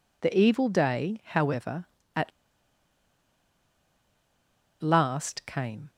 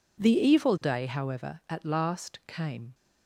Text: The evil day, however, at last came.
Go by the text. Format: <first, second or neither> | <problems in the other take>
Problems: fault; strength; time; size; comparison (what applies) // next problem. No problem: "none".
second | pauses between "at" and "last"; strong; at 2.3 s; 2.5 s long